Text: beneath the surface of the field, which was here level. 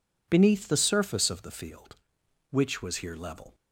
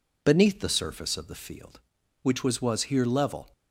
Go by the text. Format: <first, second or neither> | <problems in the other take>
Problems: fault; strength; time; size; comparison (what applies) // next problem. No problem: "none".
first | says "was" twice; at 2.6 s